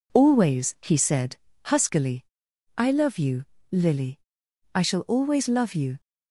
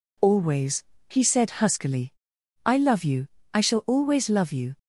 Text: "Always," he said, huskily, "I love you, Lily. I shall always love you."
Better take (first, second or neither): first